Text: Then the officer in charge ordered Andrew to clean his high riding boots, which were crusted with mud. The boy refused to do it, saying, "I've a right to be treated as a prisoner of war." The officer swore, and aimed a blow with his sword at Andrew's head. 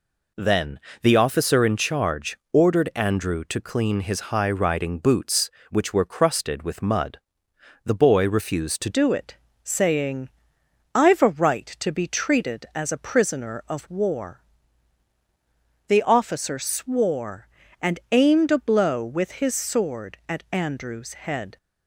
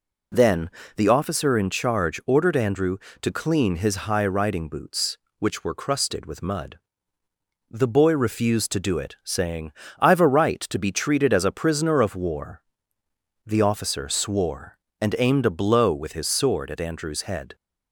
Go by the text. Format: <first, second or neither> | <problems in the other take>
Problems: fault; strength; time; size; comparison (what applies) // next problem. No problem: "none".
second | pauses between "Then" and "the"; slight; at 0.7 s; 0.22 s long; slight in the second // changes voice at "do"; from 8.8 s on; 12.7 s long